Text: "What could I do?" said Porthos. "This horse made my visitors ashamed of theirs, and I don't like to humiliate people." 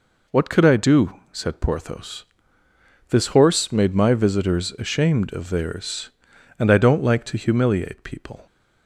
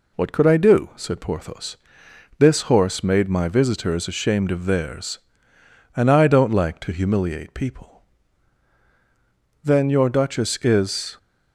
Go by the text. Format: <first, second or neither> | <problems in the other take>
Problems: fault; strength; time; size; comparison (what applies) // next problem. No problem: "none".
first | goes on to say "Then your duchess is"; from 9.6 s on; 1.5 s long